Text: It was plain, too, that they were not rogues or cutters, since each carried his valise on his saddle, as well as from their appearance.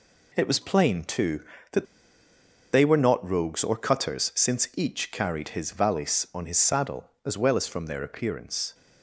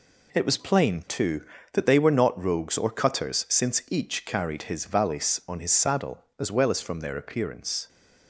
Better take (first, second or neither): second